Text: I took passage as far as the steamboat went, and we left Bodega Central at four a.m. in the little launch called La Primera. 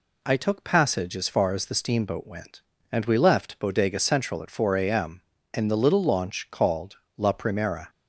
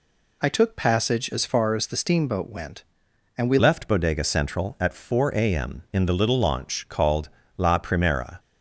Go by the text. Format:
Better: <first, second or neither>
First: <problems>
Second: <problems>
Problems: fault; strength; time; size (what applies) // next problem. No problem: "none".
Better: first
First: pauses between "called" and "La"; slight; at 6.9 s; 0.18 s long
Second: changes voice at "left"; from 3.5 s on; 4.8 s long // pauses between "called" and "La"; slight; at 7.2 s; 0.30 s long